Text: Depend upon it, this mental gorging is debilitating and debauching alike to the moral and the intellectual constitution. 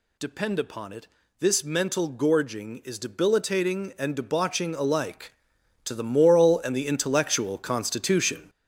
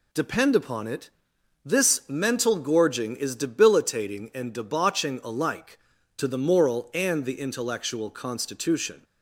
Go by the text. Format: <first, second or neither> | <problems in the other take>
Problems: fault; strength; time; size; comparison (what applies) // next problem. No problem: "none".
second | gets louder; throughout; 7 dB